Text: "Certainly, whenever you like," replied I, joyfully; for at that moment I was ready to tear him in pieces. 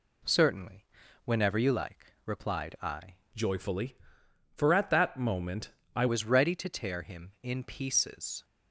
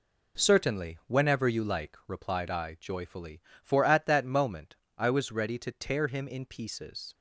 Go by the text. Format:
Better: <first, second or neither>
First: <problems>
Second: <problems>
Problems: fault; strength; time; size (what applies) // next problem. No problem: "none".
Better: second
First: changes voice from "joyfully" to "I"; from 3.3 to 6.0 s; 2.7 s long // pauses between "moment" and "I"; slight; at 5.6 s; 0.26 s long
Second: pauses between "moment" and "I"; slight; at 4.7 s; 0.22 s long